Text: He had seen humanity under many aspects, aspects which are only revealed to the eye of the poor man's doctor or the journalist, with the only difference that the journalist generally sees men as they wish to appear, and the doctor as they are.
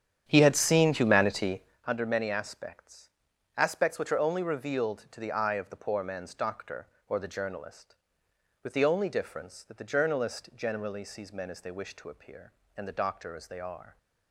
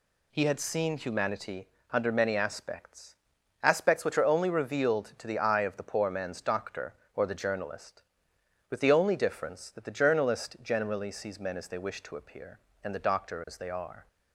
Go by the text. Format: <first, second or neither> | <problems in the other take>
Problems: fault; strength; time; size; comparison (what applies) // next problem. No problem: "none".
second | starts louder than the rest; strong; until 1.9 s; 9 dB // pauses between "humanity" and "under"; slight; at 1.6 s; 0.24 s long; slight in the second